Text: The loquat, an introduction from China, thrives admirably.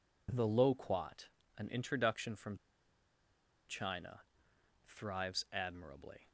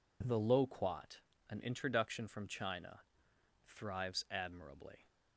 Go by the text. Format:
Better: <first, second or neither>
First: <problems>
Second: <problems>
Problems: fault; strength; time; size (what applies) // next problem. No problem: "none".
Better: second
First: pauses between "from" and "China"; at 2.5 s; 1.1 s long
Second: none